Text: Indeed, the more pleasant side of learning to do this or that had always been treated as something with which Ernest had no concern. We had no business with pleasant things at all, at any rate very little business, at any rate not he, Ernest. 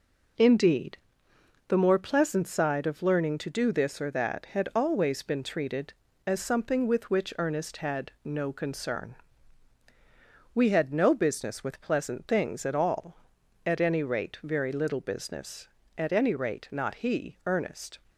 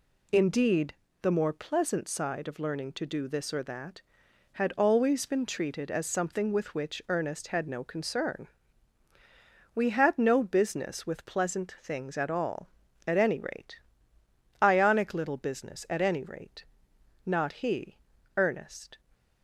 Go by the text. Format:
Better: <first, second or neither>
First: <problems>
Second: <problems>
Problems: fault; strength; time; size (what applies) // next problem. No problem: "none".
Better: first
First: none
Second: says "ionic" for "very"; at 14.6 s // pauses between "rate" and "not"; noticeable; at 16.6 s; 0.60 s long